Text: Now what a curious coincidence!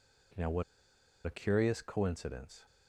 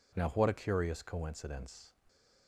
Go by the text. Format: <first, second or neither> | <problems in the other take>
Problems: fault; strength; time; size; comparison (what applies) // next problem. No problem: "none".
second | pauses between "what" and "a"; noticeable; at 0.6 s; 0.62 s long